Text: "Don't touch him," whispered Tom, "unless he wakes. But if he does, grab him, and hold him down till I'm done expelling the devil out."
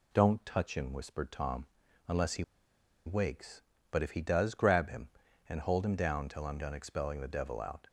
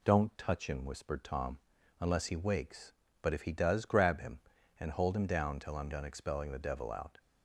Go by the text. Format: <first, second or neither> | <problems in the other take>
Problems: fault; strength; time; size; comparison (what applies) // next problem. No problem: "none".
second | pauses between "he" and "wakes"; noticeable; at 2.4 s; 0.62 s long